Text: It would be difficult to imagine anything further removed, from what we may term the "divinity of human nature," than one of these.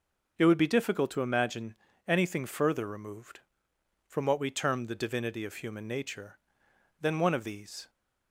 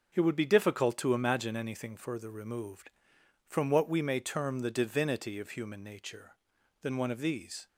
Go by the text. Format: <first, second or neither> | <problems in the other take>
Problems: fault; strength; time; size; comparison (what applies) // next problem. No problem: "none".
second | pauses between "imagine" and "anything"; slight; at 1.7 s; 0.32 s long // skips "may"; at 4.4 s